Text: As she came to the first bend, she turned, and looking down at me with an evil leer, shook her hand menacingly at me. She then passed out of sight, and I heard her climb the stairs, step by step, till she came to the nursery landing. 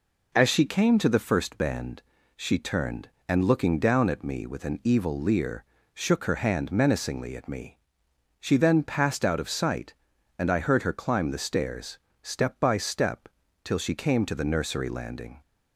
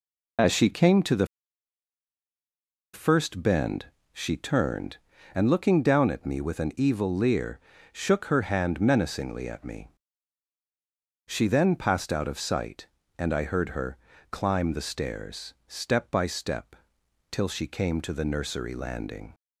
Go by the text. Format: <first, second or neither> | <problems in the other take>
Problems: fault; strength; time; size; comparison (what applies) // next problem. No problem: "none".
first | pauses between "the" and "first"; strong; at 1.2 s; 1.6 s long // pauses between "her" and "climb"; slight; at 13.9 s; 0.34 s long